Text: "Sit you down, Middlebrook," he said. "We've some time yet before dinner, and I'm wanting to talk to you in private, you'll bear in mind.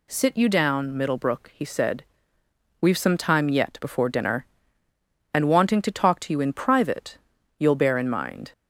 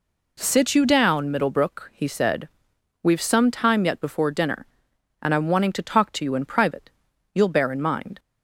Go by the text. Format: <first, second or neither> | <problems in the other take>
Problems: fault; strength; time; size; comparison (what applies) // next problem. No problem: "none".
second | skips "I'm"; at 5.4 s